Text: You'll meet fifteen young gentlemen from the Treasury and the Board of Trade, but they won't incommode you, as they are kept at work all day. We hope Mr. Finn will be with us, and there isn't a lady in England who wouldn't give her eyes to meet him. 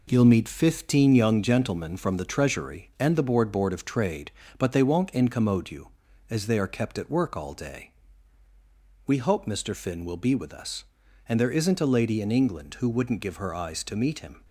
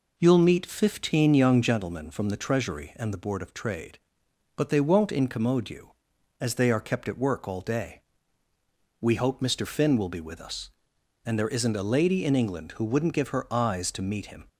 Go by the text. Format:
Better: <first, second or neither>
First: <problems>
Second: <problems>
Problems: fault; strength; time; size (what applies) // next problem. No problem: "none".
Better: second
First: says "Board" twice; at 3.5 s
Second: none